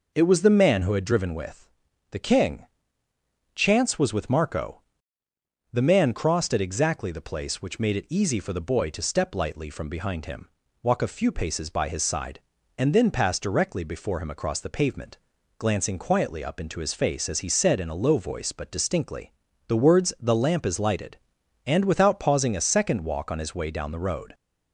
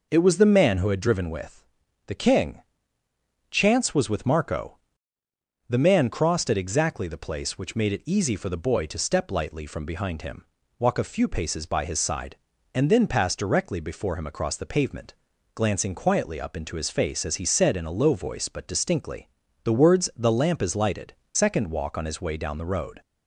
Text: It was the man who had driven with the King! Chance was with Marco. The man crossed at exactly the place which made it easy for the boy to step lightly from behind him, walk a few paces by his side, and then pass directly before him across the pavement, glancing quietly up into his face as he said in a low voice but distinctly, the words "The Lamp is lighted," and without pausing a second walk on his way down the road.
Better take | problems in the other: first | pauses between "with" and "the"; at 1.6 s; 0.44 s long; also in the first // skips "and without pausing a"; at 21.2 s

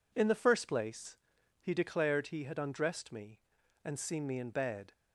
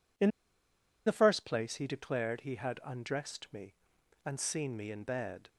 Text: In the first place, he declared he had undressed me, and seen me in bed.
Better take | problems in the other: first | pauses between "In" and "the"; noticeable; at 0.2 s; 0.76 s long

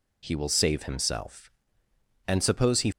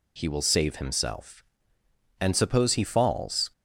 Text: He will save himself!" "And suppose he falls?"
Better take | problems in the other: second | stops before "falls"; at 2.9 s

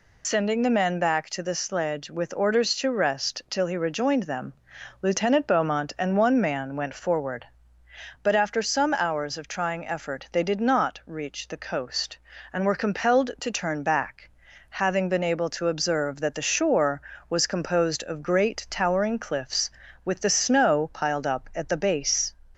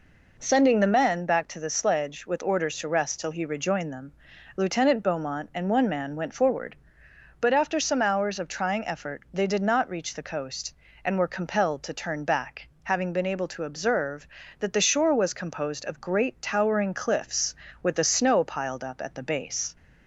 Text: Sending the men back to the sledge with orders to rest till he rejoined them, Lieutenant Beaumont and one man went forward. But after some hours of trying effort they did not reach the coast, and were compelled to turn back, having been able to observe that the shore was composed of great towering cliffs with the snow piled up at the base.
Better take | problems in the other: second | loses the start of "Sending"; at 0.2 s; 70 ms

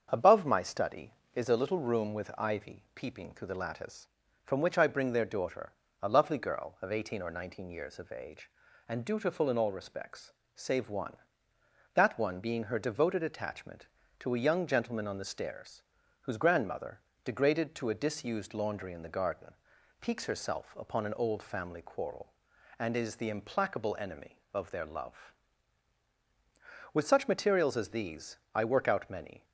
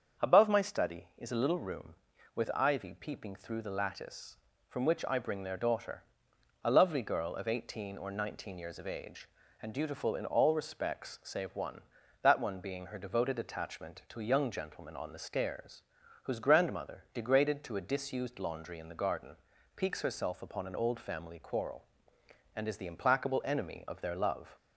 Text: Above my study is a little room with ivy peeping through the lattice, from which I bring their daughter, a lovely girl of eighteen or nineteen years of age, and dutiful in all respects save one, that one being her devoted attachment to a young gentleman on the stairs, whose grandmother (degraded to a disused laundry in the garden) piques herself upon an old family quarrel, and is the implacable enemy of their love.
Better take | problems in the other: second | starts louder than the rest; until 1.1 s; 7 dB; strong in the second // pauses between "respects" and "save"; slight; at 10.3 s; 0.24 s long // goes on to say "With such materials as these I work out many"; strong; from 26.9 s on; 2.5 s long

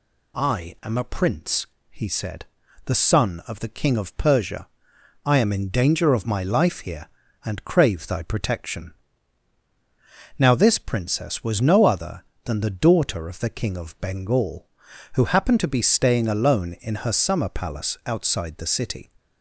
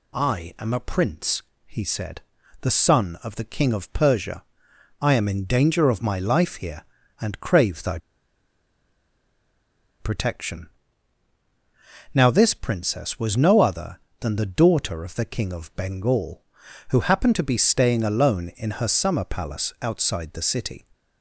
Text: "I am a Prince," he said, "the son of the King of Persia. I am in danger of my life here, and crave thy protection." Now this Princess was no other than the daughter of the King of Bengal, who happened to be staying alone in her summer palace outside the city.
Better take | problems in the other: first | pauses between "thy" and "protection"; strong; at 7.9 s; 2.0 s long

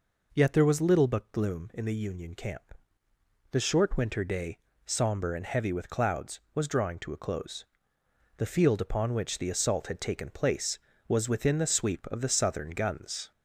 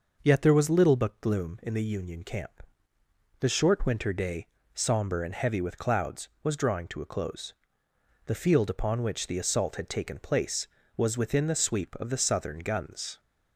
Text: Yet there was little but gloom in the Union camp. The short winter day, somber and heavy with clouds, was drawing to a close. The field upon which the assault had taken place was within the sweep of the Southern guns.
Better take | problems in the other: second | gets louder; slight; throughout; 2.5 dB

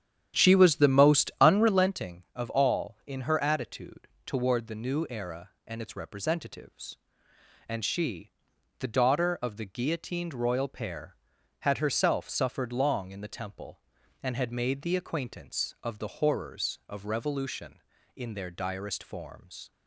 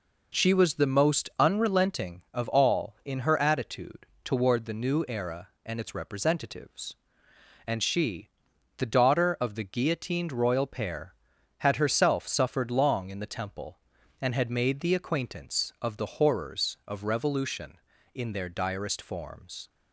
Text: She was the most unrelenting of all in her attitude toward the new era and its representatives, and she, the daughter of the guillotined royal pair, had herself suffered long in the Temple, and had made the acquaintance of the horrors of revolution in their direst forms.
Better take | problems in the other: second | starts louder than the rest; strong; until 2.0 s; 10 dB // pauses between "attitude" and "toward"; slight; at 4.0 s; 0.16 s long; slight in the second

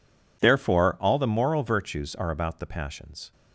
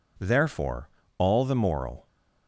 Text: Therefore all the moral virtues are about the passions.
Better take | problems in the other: first | pauses between "Therefore" and "all"; slight; at 0.8 s; 0.30 s long // stops before "virtues are about the passions"; at 2.0 s

